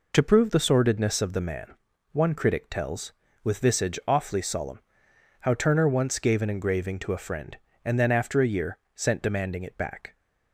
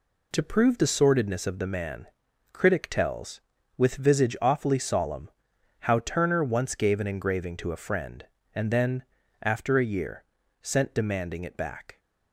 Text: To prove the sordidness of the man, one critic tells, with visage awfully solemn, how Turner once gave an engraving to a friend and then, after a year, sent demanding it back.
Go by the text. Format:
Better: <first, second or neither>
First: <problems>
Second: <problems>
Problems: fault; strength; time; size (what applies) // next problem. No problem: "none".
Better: first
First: none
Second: skips "one"; at 2.2 s